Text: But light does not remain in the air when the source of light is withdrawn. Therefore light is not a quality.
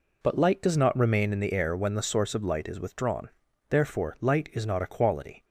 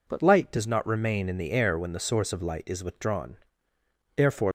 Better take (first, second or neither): first